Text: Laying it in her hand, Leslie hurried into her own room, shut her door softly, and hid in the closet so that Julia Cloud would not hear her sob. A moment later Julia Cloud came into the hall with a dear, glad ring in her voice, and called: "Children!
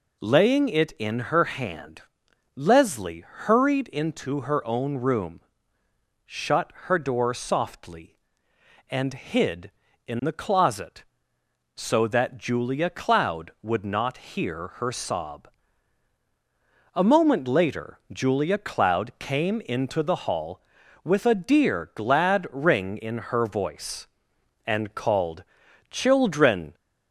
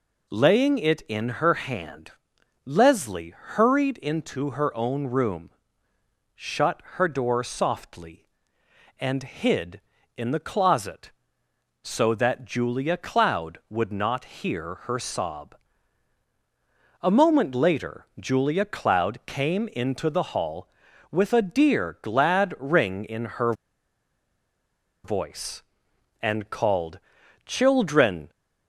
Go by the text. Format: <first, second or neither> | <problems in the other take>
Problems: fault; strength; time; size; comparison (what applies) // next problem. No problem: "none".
first | pauses between "in" and "her"; slight; at 23.2 s; 0.16 s long; slight in the first // pauses between "her" and "voice"; strong; at 23.5 s; 1.5 s long